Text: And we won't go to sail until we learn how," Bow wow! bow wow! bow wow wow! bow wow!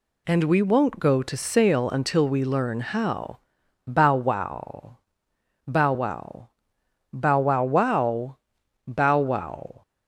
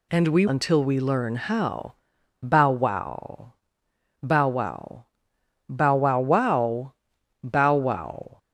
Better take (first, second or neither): first